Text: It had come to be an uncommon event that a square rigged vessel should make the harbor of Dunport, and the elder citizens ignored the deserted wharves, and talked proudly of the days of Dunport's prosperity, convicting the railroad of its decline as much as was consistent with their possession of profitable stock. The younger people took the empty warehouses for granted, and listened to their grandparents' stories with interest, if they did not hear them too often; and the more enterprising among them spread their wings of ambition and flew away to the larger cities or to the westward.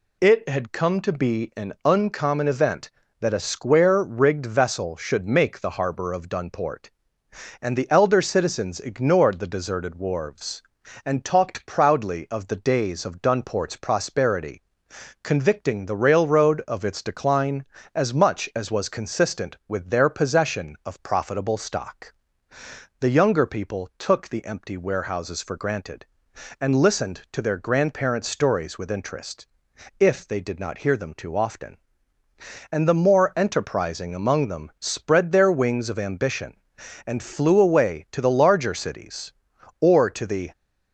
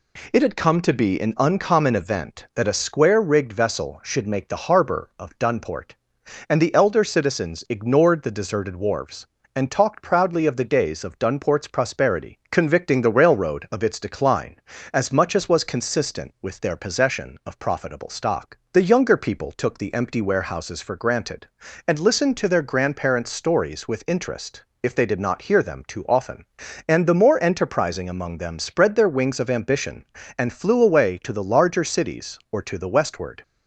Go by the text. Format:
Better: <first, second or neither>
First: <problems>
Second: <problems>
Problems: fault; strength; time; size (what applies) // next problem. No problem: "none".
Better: second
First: stops before "westward"; at 40.5 s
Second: none